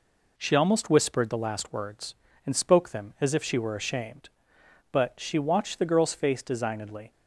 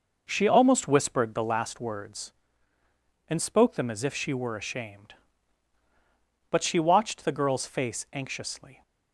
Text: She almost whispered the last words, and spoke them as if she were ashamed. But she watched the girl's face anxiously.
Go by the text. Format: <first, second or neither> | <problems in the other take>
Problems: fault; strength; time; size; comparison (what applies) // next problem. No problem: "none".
second | says "designedly" for "anxiously"; at 6.4 s